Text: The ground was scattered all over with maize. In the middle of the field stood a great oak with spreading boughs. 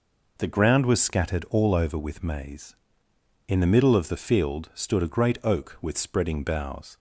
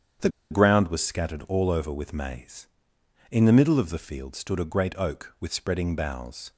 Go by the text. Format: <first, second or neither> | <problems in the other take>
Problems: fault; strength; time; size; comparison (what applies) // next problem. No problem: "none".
first | starts louder than the rest; strong; until 1.4 s; 8 dB // pauses between "The" and "ground"; slight; at 0.2 s; 0.22 s long